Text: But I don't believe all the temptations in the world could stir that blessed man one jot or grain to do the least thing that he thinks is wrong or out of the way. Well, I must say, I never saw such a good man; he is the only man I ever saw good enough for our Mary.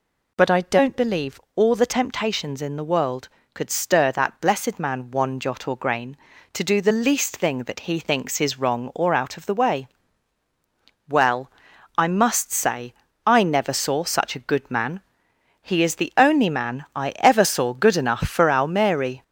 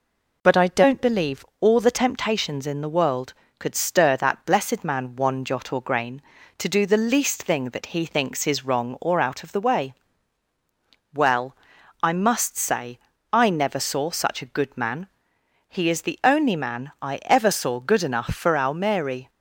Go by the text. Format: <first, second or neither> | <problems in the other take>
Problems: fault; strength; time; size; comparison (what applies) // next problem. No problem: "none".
second | gets louder; noticeable; throughout; 4.5 dB // pauses between "believe" and "all"; slight; at 1.3 s; 0.16 s long; slight in the second